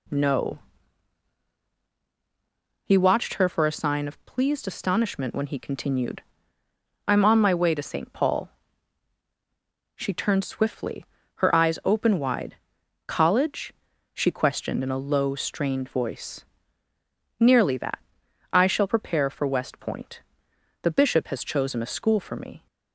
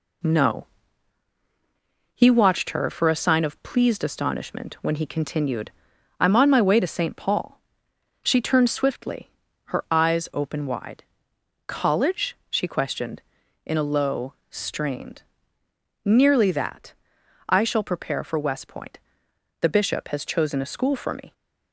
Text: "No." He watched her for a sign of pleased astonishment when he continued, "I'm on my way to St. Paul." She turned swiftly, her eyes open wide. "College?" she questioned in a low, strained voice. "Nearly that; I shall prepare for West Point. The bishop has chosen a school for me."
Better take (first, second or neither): first